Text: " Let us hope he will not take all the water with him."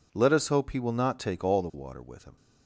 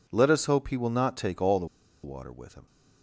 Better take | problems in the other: first | pauses between "the" and "water"; at 1.6 s; 0.37 s long

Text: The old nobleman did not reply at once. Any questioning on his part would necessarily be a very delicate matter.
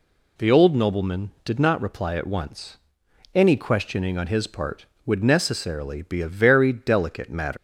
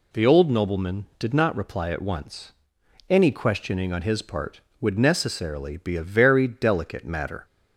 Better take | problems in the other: second | leaves "matter" unfinished; at 7.5 s; 125 ms

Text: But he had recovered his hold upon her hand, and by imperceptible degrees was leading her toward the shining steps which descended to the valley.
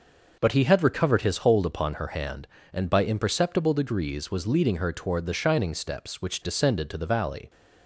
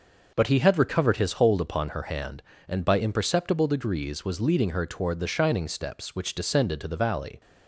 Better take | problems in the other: neither | none

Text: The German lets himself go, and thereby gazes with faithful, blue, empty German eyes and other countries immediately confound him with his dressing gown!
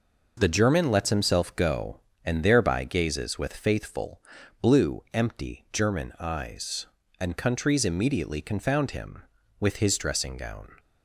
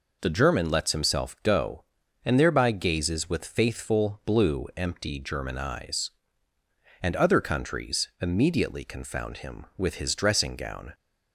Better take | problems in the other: second | skips "other"; at 7.3 s

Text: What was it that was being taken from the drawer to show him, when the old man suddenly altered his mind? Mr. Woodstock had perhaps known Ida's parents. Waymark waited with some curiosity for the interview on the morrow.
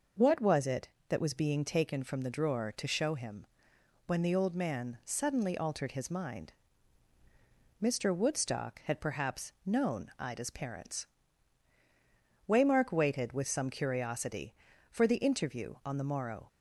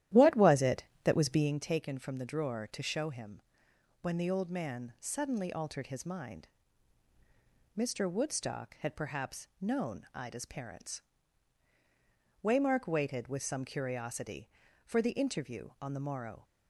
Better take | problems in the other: first | starts louder than the rest; strong; until 1.5 s; 12.5 dB

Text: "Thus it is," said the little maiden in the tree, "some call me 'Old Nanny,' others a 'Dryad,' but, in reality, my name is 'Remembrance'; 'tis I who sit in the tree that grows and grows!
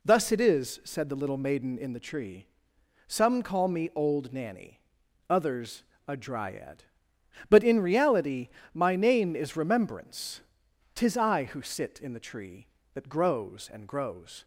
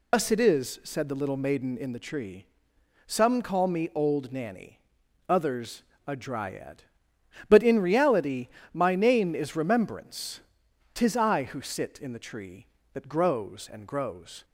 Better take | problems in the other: first | loses the start of "Thus"; at 0.1 s; 105 ms // pauses between "others" and "a"; slight; at 5.8 s; 0.24 s long; slight in the first

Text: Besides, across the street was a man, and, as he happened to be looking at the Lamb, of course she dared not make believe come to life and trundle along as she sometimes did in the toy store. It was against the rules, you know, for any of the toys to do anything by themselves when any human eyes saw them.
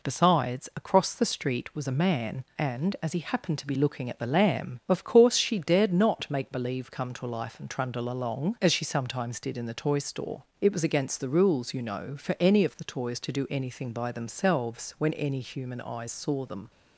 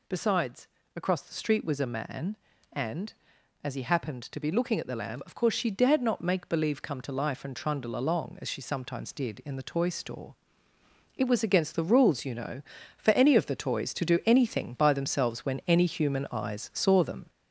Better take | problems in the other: first | gets louder; noticeable; throughout; 5 dB

